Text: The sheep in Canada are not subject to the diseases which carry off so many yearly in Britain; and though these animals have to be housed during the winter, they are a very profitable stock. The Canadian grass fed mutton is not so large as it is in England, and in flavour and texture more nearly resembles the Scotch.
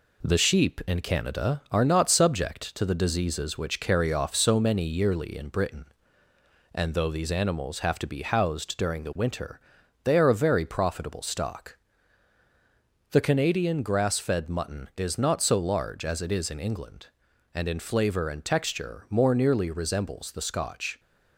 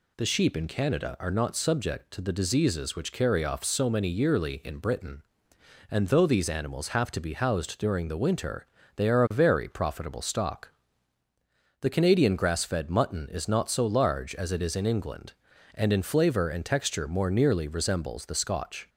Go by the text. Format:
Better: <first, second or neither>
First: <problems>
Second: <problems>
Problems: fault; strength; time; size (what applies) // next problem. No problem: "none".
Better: second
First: gets quieter; slight; throughout; 3.5 dB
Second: none